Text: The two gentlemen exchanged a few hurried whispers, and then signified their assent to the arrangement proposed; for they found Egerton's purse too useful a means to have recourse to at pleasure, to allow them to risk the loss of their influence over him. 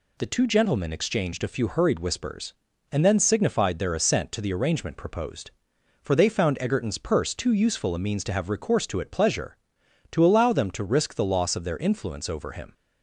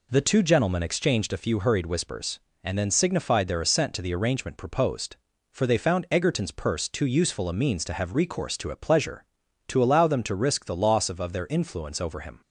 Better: first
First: none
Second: says "of" twice; at 11.2 s

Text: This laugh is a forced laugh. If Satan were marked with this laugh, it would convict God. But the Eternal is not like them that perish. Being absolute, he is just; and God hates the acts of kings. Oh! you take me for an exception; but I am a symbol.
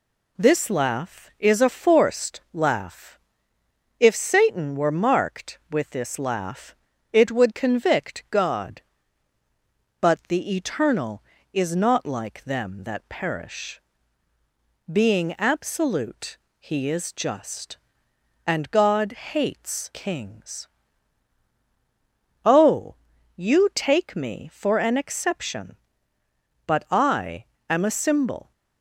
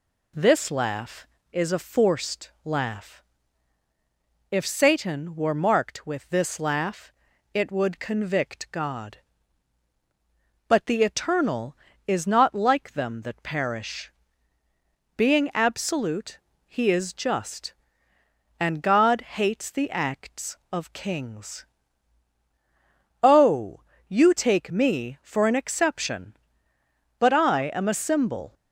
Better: second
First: skips "the acts of"; at 19.9 s // pauses between "I" and "am"; slight; at 27.4 s; 0.22 s long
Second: none

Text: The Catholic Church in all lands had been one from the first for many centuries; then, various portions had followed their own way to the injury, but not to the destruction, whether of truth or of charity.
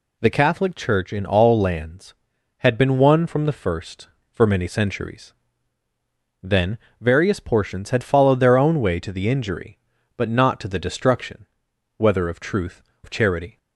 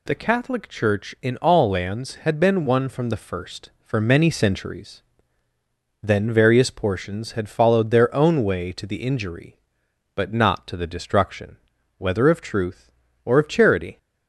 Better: second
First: skips "or"; at 12.9 s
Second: none

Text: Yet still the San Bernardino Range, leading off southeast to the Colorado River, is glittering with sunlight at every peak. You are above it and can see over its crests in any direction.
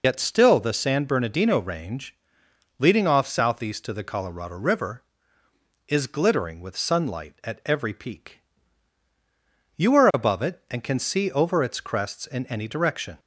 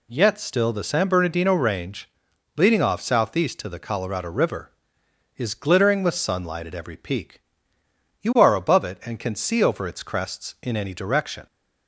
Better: second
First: loses the start of "Yet"; at 0.0 s; 70 ms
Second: none

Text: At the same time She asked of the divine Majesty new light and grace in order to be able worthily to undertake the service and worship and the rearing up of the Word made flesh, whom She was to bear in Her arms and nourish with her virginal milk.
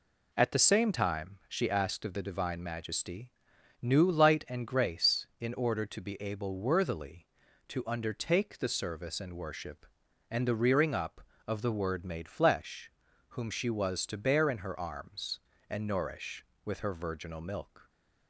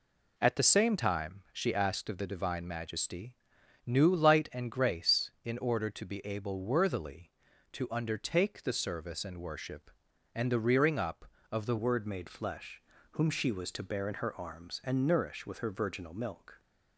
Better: first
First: pauses between "Majesty" and "new"; noticeable; at 3.2 s; 0.52 s long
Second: pauses between "Majesty" and "new"; noticeable; at 3.3 s; 0.52 s long // changes voice at "Word"; from 11.7 s on; 4.8 s long

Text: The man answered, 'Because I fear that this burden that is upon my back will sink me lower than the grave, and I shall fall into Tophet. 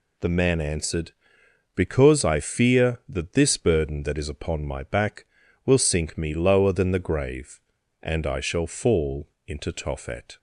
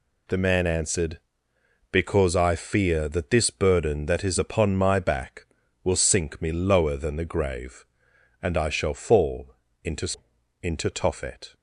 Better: first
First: pauses between "fall" and "into"; slight; at 9.2 s; 0.20 s long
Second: pauses between "fall" and "into"; slight; at 9.5 s; 0.28 s long // says "into" twice; at 10.6 s

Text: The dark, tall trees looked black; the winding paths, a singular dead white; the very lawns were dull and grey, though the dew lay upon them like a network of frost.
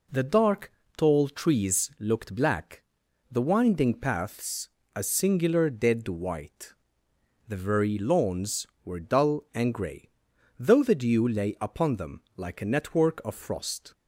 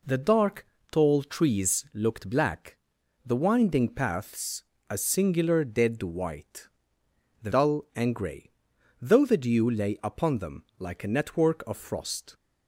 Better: first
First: none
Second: skips "very lawns were"; at 7.5 s

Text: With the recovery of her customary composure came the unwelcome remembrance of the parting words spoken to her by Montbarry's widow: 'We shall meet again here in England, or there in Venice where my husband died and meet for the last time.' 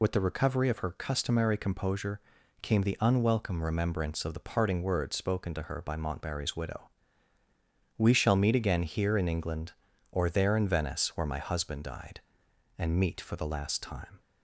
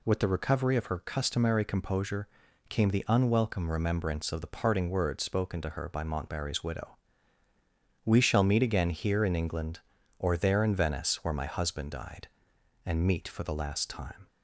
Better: second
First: loses the start of "With"; at 0.0 s; 65 ms // pauses between "composure" and "came"; at 2.1 s; 0.42 s long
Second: pauses between "composure" and "came"; at 2.2 s; 0.42 s long

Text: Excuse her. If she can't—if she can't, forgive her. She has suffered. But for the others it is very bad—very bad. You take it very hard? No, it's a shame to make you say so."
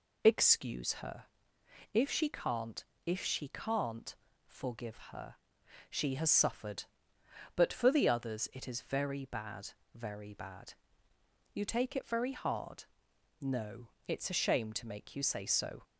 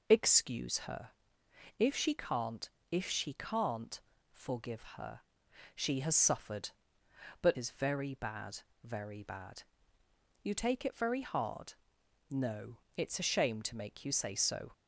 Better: first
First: none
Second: skips "for the others it"; at 7.5 s

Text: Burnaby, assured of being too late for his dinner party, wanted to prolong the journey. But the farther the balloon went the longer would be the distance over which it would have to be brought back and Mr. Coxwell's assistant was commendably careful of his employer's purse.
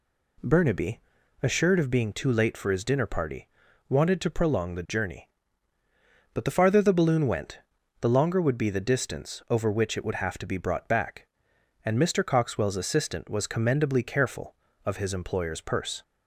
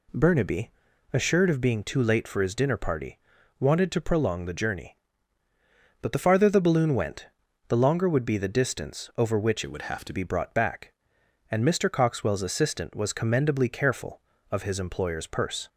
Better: first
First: pauses between "went" and "the"; at 7.5 s; 0.42 s long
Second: pauses between "went" and "the"; at 7.2 s; 0.42 s long // changes voice from "it" to "to"; from 9.6 to 10.1 s; 0.5 s long

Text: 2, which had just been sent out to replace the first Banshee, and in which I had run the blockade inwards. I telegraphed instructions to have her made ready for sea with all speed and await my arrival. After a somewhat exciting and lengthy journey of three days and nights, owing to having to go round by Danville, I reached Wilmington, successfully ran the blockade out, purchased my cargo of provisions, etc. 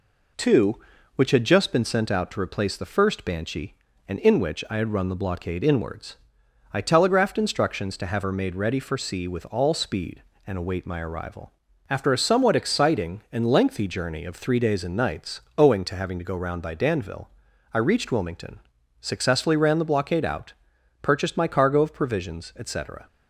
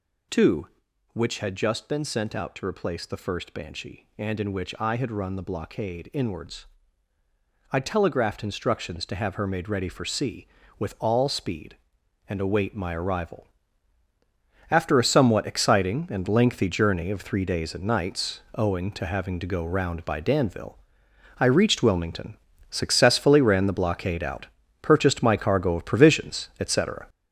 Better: first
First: none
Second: gets louder; throughout; 7 dB

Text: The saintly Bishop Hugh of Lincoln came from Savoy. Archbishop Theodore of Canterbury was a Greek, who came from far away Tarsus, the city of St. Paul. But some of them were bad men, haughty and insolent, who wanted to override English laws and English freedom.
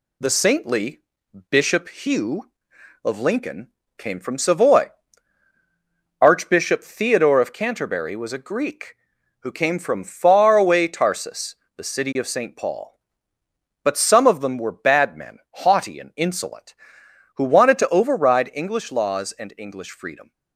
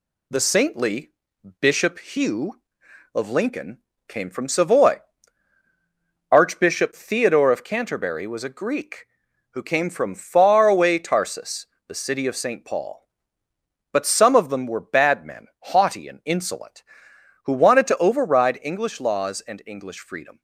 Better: neither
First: pauses between "saintly" and "Bishop"; noticeable; at 1.0 s; 0.50 s long // pauses between "Lincoln" and "came"; slight; at 3.6 s; 0.32 s long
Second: pauses between "saintly" and "Bishop"; noticeable; at 1.1 s; 0.50 s long // pauses between "Lincoln" and "came"; slight; at 3.7 s; 0.32 s long

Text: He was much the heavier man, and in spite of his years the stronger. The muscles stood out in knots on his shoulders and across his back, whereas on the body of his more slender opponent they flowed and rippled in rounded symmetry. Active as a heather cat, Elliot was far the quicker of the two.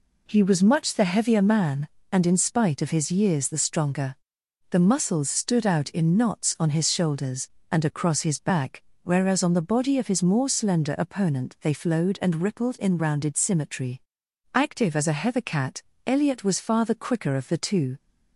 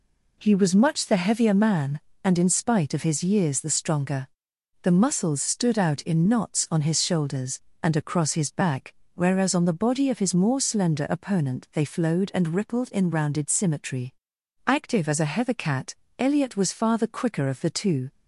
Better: neither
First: none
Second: none

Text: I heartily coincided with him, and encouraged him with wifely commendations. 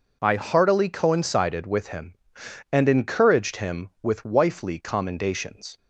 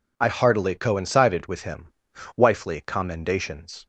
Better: first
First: none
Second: skips "and encouraged him with"; at 2.1 s

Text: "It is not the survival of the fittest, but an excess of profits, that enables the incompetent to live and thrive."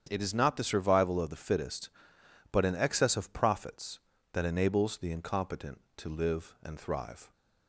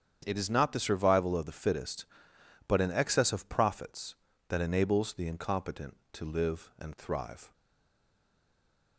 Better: first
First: starts louder than the rest; strong; until 1.1 s; 8.5 dB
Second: starts louder than the rest; strong; until 1.2 s; 8.5 dB // stays silent after the last word; noticeable; from 7.5 s on; 1.4 s long

